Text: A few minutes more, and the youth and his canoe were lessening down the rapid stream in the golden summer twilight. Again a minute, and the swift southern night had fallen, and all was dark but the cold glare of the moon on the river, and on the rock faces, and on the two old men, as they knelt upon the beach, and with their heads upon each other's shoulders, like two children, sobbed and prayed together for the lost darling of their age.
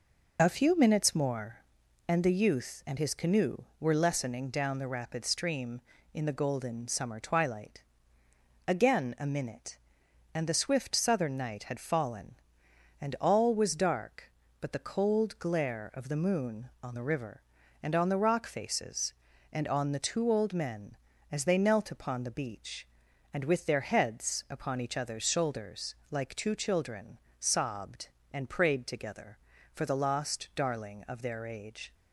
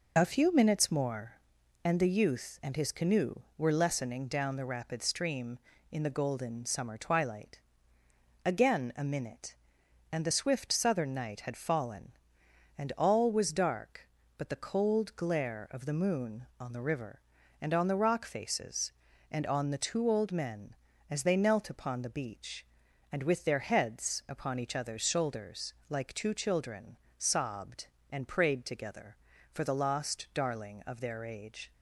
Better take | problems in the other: neither | none

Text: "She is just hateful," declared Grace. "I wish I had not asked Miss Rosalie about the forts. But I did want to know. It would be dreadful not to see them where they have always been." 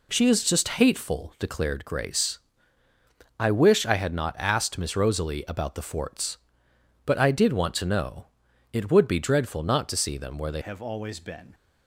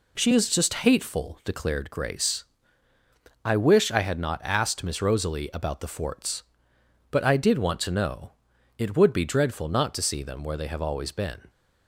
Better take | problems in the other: second | changes voice at "have"; from 10.6 s on; 0.9 s long

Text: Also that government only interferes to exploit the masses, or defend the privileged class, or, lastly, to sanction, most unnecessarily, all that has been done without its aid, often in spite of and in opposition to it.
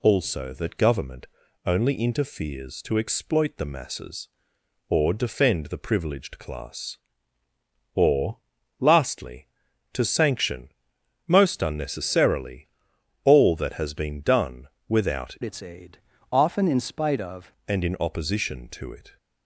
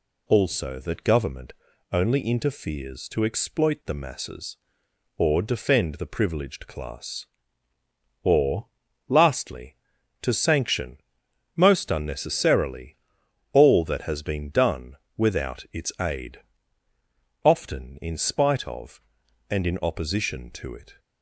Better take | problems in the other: second | pauses between "government" and "only"; at 1.2 s; 0.40 s long; also in the second // pauses between "done" and "without"; slight; at 14.6 s; 0.22 s long; slight in the second // changes voice from "its" to "of"; from 15.4 to 17.5 s; 2.1 s long

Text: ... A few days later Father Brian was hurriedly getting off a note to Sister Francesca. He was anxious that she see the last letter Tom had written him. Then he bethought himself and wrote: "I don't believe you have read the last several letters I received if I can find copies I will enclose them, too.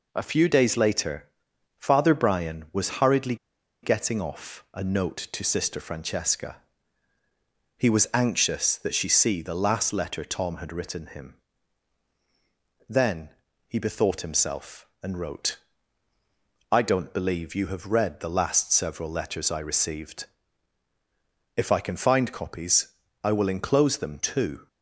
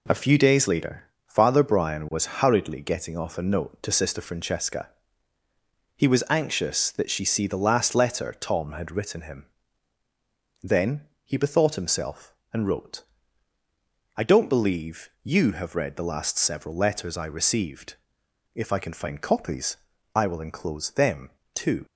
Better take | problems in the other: second | pauses between "later" and "Father"; noticeable; at 1.2 s; 0.50 s long; slight in the second // pauses between "hurriedly" and "getting"; noticeable; at 3.3 s; 0.46 s long // pauses between "Then" and "he"; slight; at 13.3 s; 0.36 s long; slight in the second // pauses between "received" and "if"; strong; at 20.2 s; 1.3 s long; noticeable in the second // pauses between "copies" and "I"; at 22.8 s; 0.38 s long; also in the second

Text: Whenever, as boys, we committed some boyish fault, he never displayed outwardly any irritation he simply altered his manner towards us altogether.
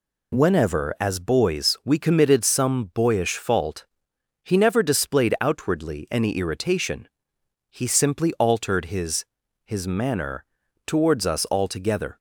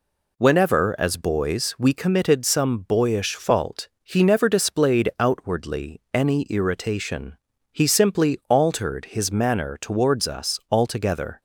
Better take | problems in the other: second | pauses between "irritation" and "he"; noticeable; at 7.0 s; 0.62 s long; slight in the second // says "his" twice; at 9.6 s // pauses between "manner" and "towards"; at 10.4 s; 0.44 s long

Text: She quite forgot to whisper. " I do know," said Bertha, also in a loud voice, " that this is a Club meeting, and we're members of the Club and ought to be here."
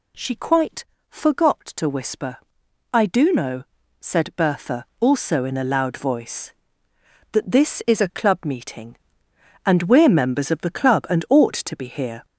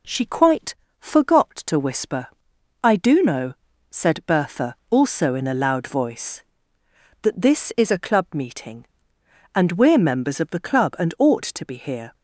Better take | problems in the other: second | gets louder; throughout; 7 dB // pauses between "quite" and "forgot"; slight; at 0.8 s; 0.24 s long; slight in the second

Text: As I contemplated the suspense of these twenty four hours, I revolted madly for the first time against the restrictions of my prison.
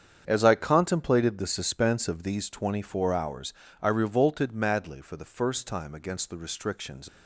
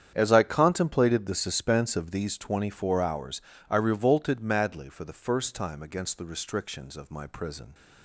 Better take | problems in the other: second | starts louder than the rest; strong; until 1.2 s; 8 dB; strong in the second // stops before "of my prison"; at 7.0 s

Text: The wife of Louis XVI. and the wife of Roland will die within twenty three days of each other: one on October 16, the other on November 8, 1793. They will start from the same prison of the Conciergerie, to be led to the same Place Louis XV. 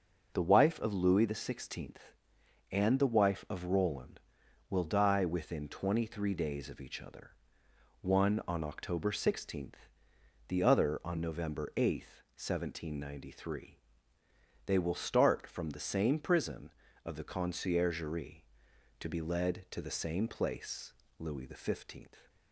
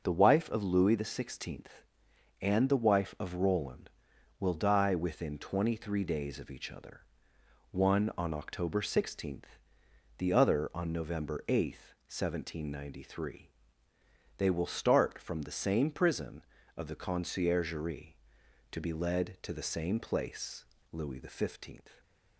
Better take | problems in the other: neither | pauses between "Place" and "Louis"; slight; the same in both

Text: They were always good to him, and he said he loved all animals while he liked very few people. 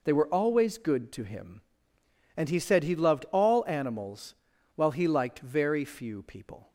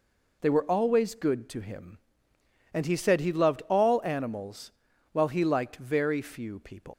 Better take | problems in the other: first | pauses between "animals" and "while"; at 4.7 s; 0.42 s long; also in the first // leaves "people" unfinished; at 6.9 s; 150 ms

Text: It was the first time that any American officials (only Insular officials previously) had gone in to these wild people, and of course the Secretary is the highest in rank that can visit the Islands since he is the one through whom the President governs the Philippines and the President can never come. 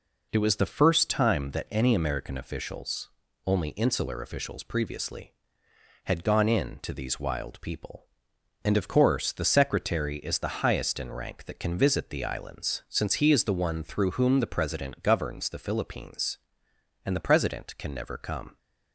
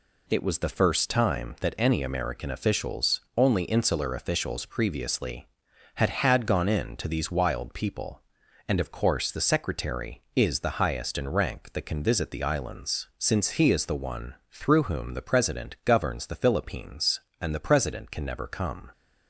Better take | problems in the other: first | says "had" twice; at 6.0 s // pauses between "one" and "through"; slight; at 14.3 s; 0.16 s long

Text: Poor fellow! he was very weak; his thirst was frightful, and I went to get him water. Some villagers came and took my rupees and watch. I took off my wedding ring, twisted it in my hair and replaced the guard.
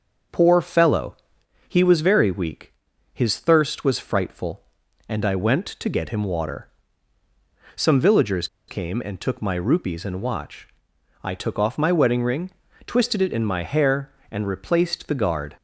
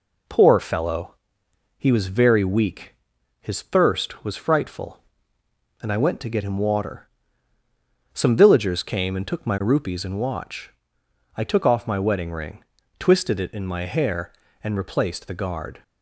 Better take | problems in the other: second | starts louder than the rest; until 1.8 s; 6.5 dB // pauses between "villagers" and "came"; slight; at 8.4 s; 0.21 s long

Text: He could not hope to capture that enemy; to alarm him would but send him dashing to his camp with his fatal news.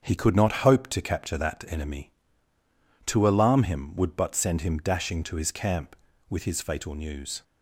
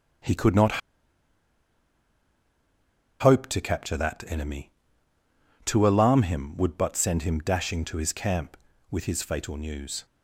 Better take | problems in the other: first | starts louder than the rest; strong; until 3.6 s; 7 dB; strong in the first // pauses between "not" and "hope"; strong; at 0.8 s; 2.4 s long

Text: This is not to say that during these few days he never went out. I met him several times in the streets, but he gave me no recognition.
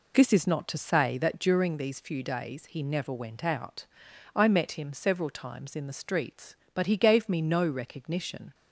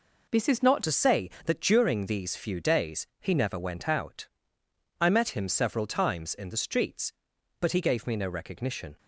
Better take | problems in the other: first | changes voice at "to"; from 0.8 s on; 8.1 s long

